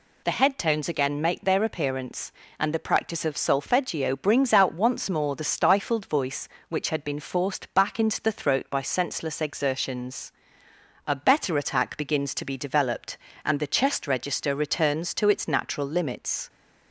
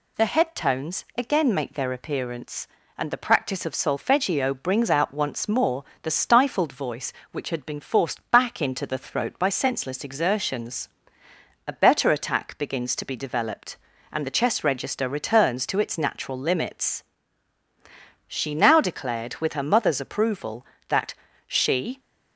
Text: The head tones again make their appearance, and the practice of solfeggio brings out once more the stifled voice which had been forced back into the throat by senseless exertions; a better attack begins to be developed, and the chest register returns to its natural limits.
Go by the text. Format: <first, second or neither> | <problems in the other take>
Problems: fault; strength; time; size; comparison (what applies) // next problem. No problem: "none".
first | pauses between "more" and "the"; slight; at 5.8 s; 0.18 s long // goes on to say "She now declared with her mother's approval that she"; strong; from 18.2 s on; 3.7 s long